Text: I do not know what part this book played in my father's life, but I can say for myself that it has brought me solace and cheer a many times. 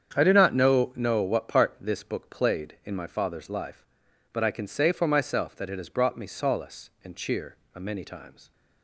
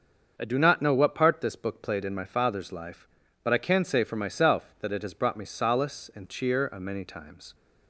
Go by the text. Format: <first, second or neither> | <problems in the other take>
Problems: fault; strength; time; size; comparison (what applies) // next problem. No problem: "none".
second | starts louder than the rest; strong; until 1.1 s; 8 dB; also in the second // says "know" twice; at 0.9 s // pauses between "cheer" and "a"; slight; at 7.5 s; 0.18 s long